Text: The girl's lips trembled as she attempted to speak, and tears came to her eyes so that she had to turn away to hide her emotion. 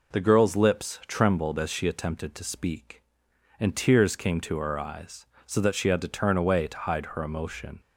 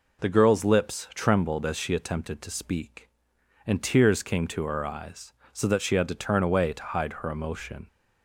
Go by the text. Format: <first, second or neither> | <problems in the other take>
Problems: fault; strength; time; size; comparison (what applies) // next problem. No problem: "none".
neither | none